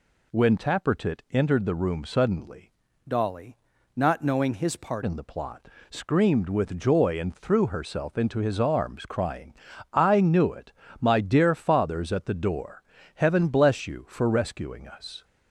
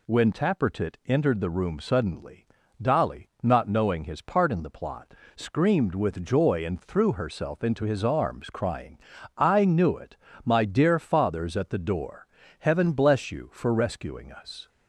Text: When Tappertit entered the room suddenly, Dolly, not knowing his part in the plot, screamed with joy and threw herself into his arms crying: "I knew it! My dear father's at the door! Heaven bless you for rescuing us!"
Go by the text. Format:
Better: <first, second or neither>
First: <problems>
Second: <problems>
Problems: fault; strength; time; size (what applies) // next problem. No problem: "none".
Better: second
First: changes voice from "Dolly" to "part"; from 3.0 to 5.0 s; 2.0 s long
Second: none